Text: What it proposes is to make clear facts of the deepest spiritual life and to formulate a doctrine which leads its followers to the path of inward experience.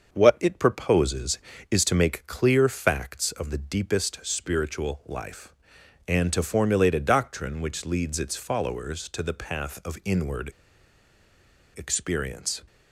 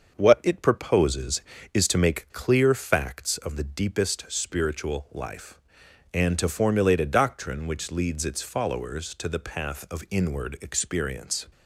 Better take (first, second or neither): second